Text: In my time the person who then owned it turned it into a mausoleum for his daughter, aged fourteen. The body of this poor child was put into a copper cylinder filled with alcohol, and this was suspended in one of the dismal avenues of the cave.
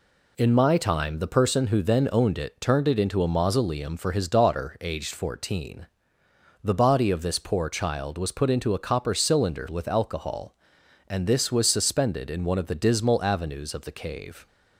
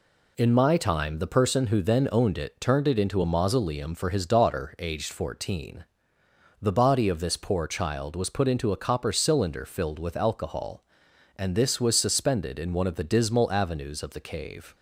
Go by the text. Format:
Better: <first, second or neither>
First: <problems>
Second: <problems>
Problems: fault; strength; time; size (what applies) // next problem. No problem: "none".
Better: second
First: skips "filled"; at 9.6 s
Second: none